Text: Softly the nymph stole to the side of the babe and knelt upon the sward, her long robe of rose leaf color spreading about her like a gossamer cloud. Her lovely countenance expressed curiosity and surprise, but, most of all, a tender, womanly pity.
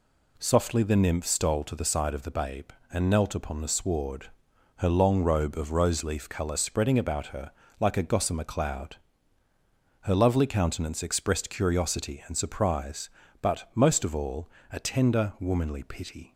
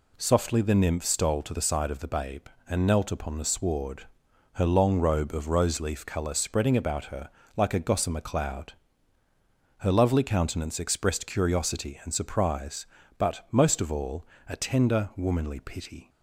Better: neither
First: pauses between "her" and "like"; slight; at 7.5 s; 0.26 s long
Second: pauses between "her" and "like"; slight; at 7.3 s; 0.24 s long

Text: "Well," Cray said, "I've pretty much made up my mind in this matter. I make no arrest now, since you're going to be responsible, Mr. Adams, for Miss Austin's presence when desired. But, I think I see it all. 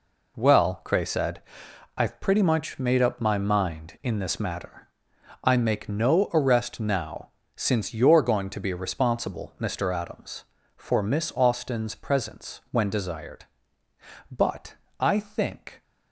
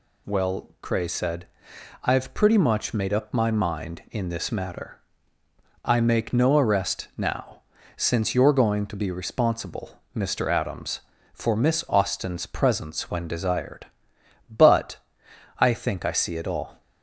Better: second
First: stops before "I see it all"; at 15.8 s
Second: none

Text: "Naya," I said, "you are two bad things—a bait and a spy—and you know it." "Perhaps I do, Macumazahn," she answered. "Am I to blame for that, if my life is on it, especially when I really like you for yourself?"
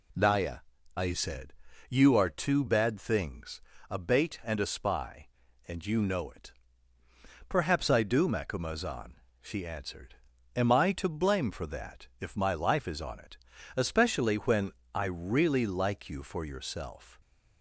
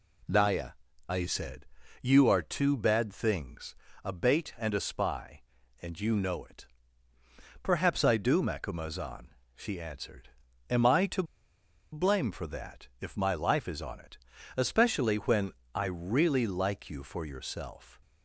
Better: first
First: pauses between "when" and "I"; slight; at 14.7 s; 0.24 s long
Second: pauses between "to" and "blame"; noticeable; at 11.2 s; 0.69 s long // pauses between "when" and "I"; slight; at 15.5 s; 0.24 s long

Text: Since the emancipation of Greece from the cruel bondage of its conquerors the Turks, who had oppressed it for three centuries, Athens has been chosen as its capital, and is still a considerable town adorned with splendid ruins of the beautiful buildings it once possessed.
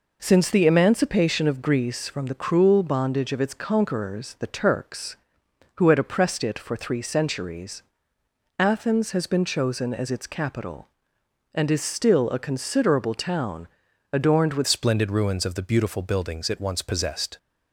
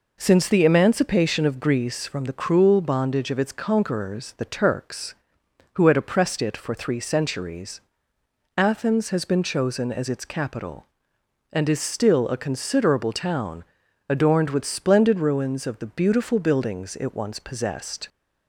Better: second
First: pauses between "town" and "adorned"; noticeable; at 13.6 s; 0.46 s long // changes voice at "splendid"; from 14.6 s on; 2.7 s long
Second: pauses between "town" and "adorned"; noticeable; at 13.6 s; 0.46 s long

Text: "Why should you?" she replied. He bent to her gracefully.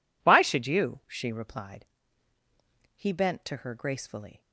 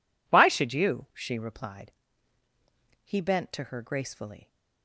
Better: neither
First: none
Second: none

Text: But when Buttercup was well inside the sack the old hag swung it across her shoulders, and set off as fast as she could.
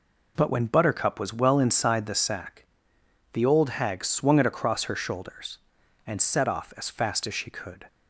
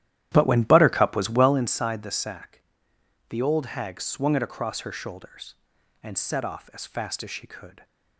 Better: first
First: pauses between "sack" and "the"; noticeable; at 2.6 s; 0.70 s long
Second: starts louder than the rest; strong; until 1.6 s; 12.5 dB // pauses between "sack" and "the"; noticeable; at 2.5 s; 0.70 s long

